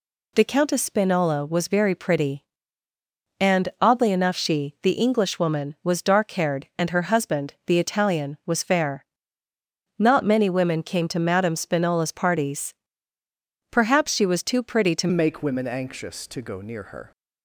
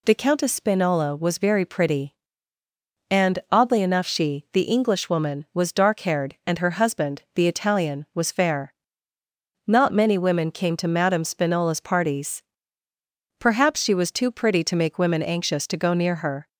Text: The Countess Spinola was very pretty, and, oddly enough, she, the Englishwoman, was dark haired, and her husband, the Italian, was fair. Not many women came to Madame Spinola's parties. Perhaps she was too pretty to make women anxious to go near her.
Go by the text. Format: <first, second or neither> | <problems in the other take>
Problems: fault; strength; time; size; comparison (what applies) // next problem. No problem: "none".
second | changes voice at "make"; from 15.1 s on; 2.0 s long